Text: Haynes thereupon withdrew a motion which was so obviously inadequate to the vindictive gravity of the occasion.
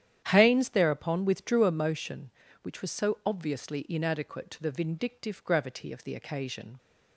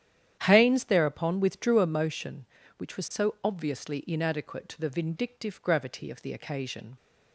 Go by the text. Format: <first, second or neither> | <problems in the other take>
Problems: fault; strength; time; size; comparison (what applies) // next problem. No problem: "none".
neither | starts louder than the rest; strong; the same in both